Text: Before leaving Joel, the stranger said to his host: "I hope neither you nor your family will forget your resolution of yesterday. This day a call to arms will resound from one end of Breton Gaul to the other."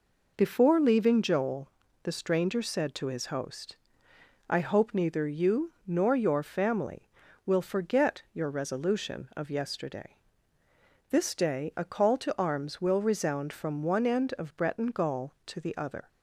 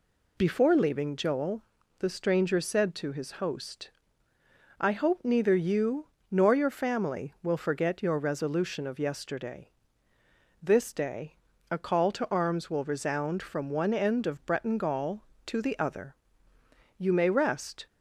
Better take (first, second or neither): first